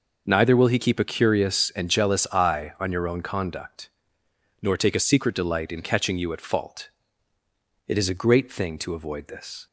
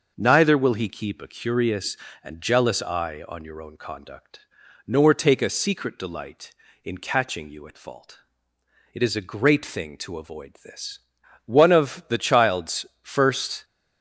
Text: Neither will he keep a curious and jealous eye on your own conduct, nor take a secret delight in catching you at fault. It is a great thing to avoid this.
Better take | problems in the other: first | starts louder than the rest; until 1.1 s; 6 dB // goes on to say "One of the child's first"; strong; from 11.4 s on; 2.1 s long

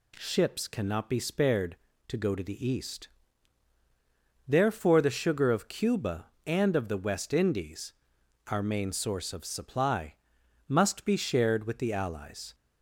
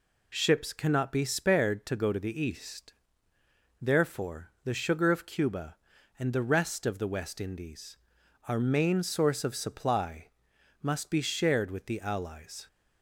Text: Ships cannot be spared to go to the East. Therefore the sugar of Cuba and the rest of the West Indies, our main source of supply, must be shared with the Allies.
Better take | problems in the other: second | skips "the rest"; at 6.7 s

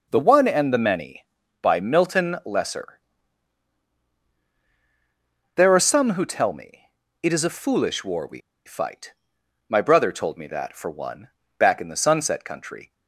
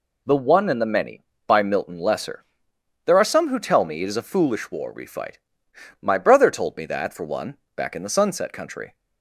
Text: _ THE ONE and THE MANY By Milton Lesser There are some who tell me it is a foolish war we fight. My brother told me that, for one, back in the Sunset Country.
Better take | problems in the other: second | pauses between "Lesser" and "There"; strong; at 2.9 s; 2.5 s long; noticeable in the second // pauses between "me" and "it"; at 6.8 s; 0.38 s long // pauses between "we" and "fight"; slight; at 8.3 s; 0.25 s long

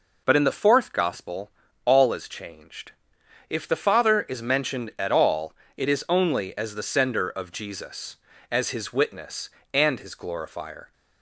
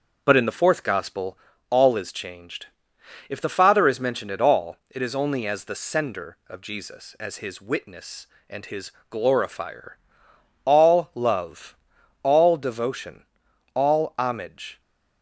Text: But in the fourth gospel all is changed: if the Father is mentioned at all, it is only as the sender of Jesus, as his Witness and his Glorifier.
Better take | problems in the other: first | starts louder than the rest; until 1.2 s; 6.5 dB // pauses between "gospel" and "all"; slight; at 1.3 s; 0.32 s long; slight in the first // pauses between "his" and "Glorifier"; slight; at 8.8 s; 0.20 s long // goes on to say "All love all devotion all homage"; strong; from 10.6 s on; 4.1 s long

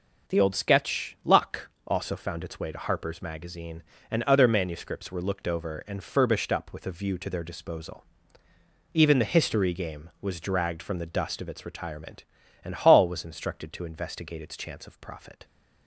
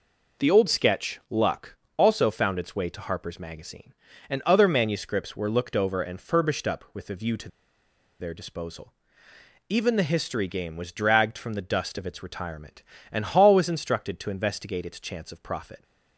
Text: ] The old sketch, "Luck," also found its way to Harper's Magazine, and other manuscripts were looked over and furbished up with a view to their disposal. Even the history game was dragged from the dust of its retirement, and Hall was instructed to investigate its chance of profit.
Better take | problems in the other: first | pauses between "to" and "their"; noticeable; at 7.4 s; 0.71 s long

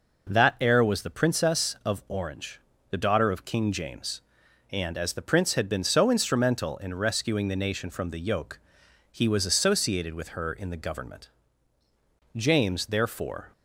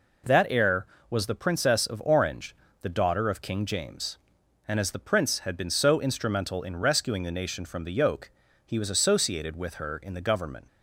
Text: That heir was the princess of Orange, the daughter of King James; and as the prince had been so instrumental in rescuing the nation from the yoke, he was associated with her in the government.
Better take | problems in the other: second | goes on to say "James therefore"; noticeable; from 12.3 s on; 1.1 s long

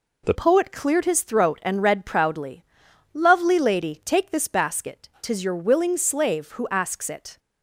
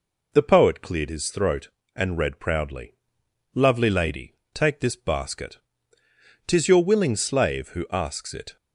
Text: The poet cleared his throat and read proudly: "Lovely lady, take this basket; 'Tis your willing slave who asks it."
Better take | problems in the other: second | changes voice at "poet"; from 0.3 s on; 7.0 s long

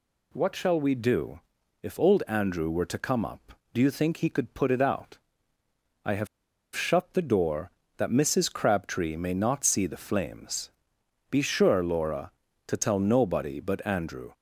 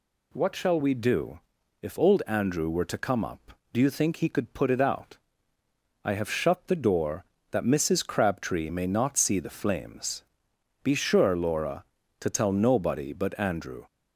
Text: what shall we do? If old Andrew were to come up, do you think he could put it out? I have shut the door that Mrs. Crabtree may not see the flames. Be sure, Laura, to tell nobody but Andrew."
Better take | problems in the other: second | pauses between "have" and "shut"; noticeable; at 6.2 s; 0.48 s long

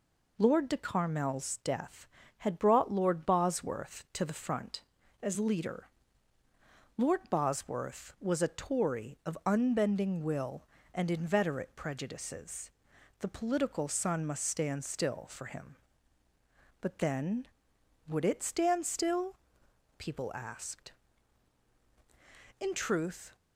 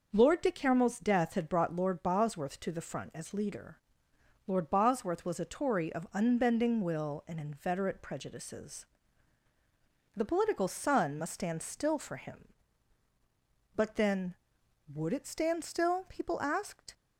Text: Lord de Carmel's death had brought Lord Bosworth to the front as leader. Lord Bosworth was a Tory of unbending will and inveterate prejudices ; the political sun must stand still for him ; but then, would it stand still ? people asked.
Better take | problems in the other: second | goes on to say "In truth"; noticeable; from 22.5 s on; 0.76 s long

